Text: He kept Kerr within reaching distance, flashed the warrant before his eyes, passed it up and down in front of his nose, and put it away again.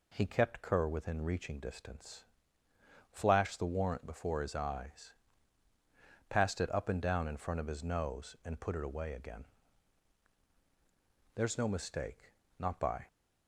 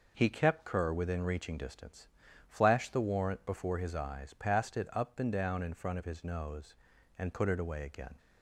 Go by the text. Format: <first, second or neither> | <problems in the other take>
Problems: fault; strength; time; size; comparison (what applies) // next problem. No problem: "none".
second | goes on to say "There's no mistake not by"; strong; from 11.3 s on; 1.7 s long